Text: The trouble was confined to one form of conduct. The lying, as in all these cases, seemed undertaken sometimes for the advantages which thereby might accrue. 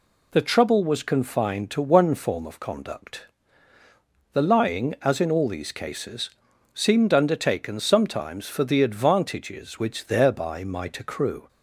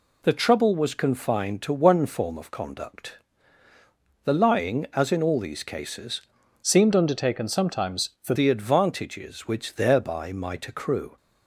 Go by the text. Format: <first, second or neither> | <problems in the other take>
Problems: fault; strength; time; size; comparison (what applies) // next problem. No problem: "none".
first | changes voice from "seemed" to "for"; from 6.6 to 8.3 s; 1.7 s long